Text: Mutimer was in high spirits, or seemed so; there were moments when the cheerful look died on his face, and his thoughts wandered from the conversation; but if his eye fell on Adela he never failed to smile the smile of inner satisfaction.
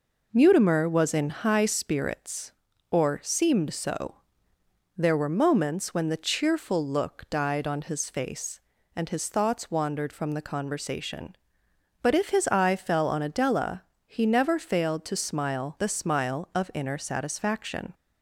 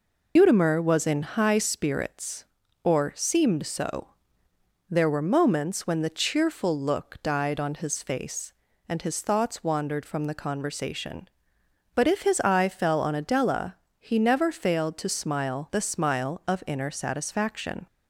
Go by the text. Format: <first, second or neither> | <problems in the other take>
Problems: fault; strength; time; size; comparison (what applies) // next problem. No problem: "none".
first | loses the start of "Mutimer"; at 0.3 s; 110 ms // pauses between "Adela" and "he"; slight; at 13.7 s; 0.24 s long; slight in the first